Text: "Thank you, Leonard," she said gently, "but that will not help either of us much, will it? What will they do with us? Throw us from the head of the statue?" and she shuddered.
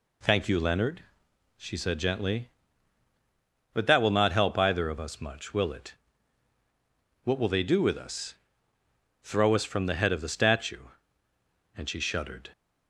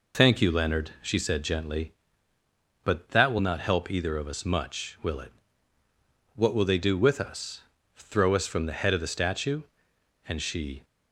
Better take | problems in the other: first | stops before "shuddered"; at 10.8 s

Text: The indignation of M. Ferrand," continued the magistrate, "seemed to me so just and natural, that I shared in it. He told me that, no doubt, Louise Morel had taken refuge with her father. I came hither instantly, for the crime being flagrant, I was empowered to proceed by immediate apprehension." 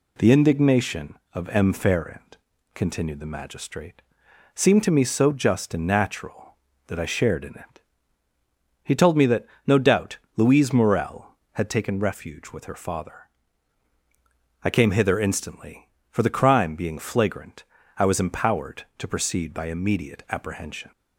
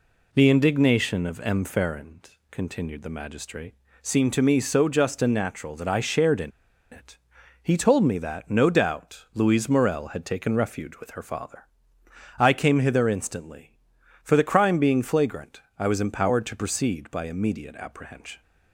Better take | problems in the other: first | pauses between "in" and "it"; at 6.5 s; 0.42 s long

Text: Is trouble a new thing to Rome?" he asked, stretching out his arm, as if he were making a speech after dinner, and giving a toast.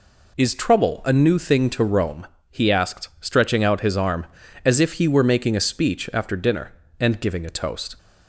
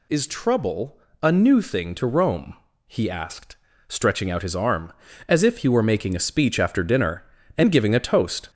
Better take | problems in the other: first | gets louder; throughout; 4 dB // pauses between "trouble" and "a"; slight; at 0.9 s; 0.24 s long

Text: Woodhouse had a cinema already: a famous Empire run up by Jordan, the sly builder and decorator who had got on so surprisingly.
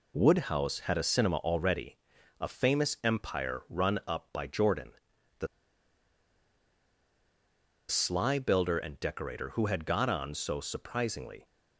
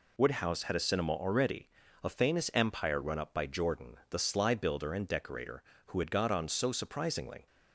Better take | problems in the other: second | pauses between "the" and "sly"; strong; at 5.4 s; 2.4 s long

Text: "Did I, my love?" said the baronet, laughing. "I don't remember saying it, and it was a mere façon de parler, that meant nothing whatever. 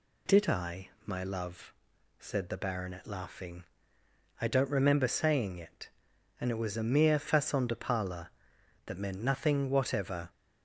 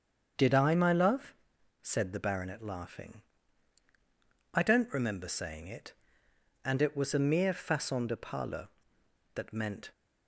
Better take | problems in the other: first | starts louder than the rest; until 1.8 s; 7 dB // stops before "nothing whatever"; at 9.9 s

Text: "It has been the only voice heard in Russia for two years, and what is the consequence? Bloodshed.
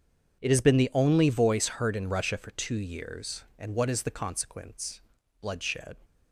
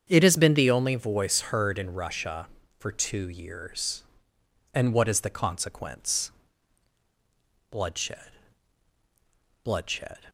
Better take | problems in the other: first | starts louder than the rest; strong; until 1.0 s; 7.5 dB // says "Bloodshed" twice; at 9.6 s

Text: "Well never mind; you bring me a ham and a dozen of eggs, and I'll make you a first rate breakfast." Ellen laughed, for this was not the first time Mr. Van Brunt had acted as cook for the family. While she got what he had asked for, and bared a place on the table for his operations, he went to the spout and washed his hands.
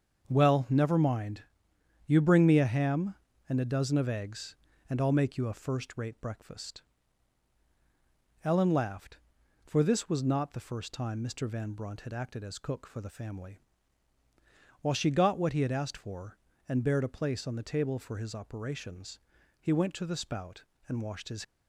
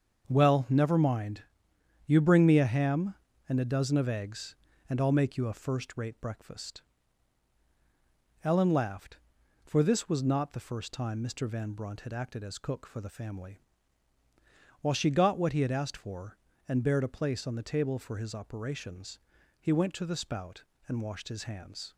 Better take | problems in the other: second | starts louder than the rest; until 1.3 s; 6.5 dB; also in the second // stops before "hands"; at 21.4 s

